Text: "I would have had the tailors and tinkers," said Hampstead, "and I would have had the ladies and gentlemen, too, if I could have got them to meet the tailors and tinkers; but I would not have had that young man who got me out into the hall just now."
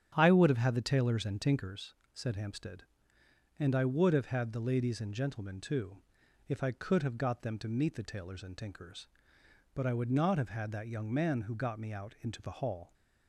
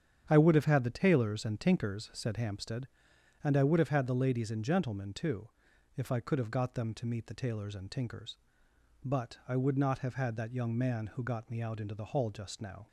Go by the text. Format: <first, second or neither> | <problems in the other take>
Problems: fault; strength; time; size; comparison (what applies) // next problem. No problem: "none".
second | starts louder than the rest; strong; until 1.1 s; 9.5 dB; strong in the second // stops before "just now"; at 12.9 s